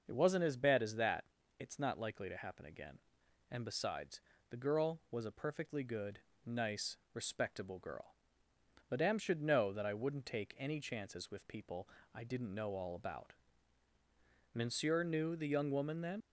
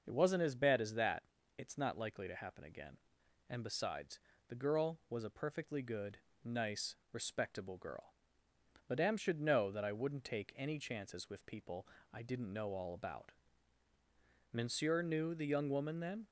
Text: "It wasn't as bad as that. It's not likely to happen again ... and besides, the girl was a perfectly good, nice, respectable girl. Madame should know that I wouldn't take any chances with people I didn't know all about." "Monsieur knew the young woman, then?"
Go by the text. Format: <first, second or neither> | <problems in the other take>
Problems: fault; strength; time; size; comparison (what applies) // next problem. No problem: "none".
second | starts louder than the rest; noticeable; until 1.0 s; 6 dB; noticeable in the second // pauses between "people" and "I"; slight; at 11.8 s; 0.28 s long; slight in the second // leaves "then" unfinished; at 16.2 s; 90 ms